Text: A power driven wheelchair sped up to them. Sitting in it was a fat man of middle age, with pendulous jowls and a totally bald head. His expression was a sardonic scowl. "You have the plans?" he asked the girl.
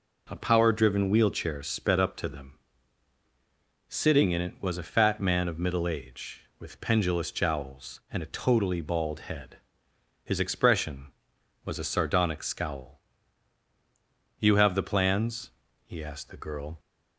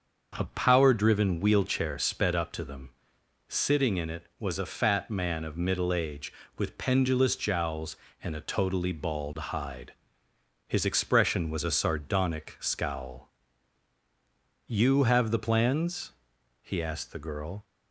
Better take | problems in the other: first | starts louder than the rest; until 1.3 s; 6.5 dB // says "hide" for "head"; at 9.3 s

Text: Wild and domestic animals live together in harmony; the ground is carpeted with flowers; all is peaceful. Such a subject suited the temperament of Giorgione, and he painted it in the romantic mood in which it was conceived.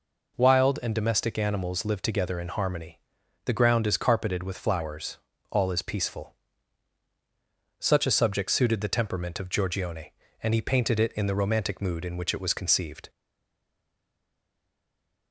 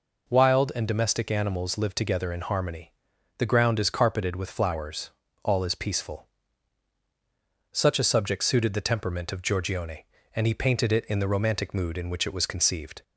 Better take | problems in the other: second | stays silent after the last word; from 13.0 s on; 2.3 s long

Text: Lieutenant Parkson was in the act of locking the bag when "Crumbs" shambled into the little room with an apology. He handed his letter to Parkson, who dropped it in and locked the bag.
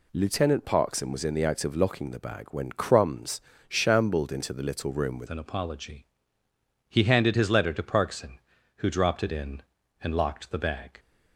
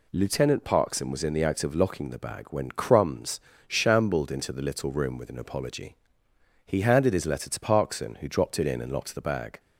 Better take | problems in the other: second | pauses between "Crumbs" and "shambled"; slight; at 3.3 s; 0.28 s long; slight in the second // changes voice at "an"; from 5.2 s on; 5.7 s long

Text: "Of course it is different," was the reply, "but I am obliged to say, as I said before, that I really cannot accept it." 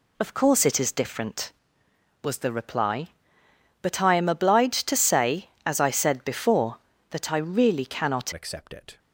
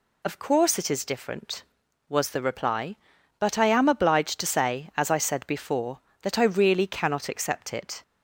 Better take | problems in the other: second | changes voice at "accept"; from 8.3 s on; 0.6 s long

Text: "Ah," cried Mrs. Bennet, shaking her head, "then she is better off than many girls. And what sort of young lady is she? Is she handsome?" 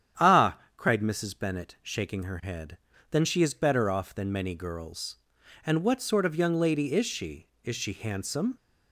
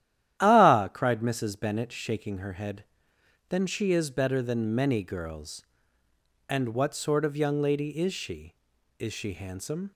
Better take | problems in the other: first | starts louder than the rest; strong; until 1.4 s; 12 dB; strong in the first // skips "off"; at 4.4 s

